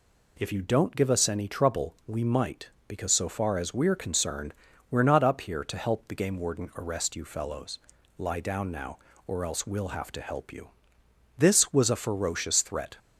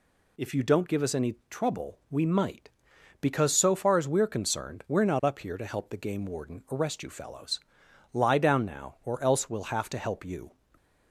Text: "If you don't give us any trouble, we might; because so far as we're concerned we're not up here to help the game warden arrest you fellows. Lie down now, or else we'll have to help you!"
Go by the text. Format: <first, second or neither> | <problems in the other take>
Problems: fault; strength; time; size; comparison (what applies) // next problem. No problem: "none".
second | pauses between "concerned" and "we're"; at 4.5 s; 0.36 s long // goes on to say "This was a ferocious threat"; from 11.3 s on; 1.6 s long